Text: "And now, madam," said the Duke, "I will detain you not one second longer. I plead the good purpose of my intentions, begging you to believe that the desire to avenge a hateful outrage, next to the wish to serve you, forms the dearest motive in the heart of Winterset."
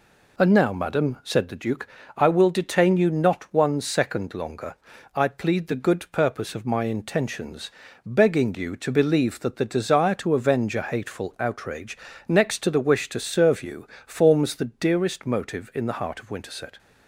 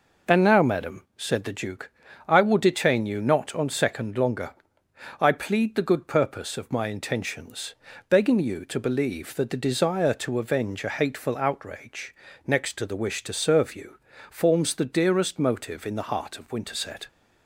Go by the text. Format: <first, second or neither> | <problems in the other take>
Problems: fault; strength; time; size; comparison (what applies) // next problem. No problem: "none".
first | says "on" for "one"; at 3.5 s